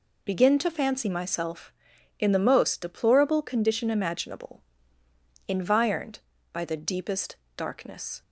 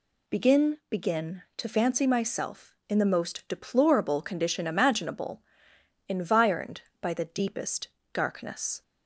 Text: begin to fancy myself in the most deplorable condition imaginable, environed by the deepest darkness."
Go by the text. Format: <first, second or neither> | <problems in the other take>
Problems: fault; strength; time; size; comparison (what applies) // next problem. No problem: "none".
first | says "begin" twice; at 0.9 s // pauses between "deepest" and "darkness"; slight; at 7.8 s; 0.24 s long; slight in the first